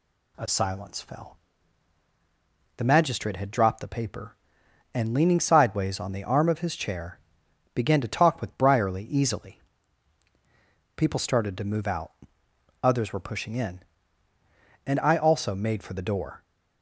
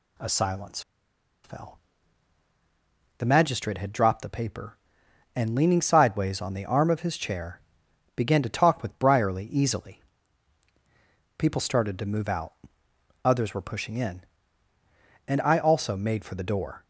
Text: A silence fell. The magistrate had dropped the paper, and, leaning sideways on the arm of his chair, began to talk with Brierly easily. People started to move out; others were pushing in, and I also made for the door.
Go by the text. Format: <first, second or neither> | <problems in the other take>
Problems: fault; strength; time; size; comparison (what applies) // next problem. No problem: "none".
first | pauses between "silence" and "fell"; noticeable; at 0.8 s; 0.63 s long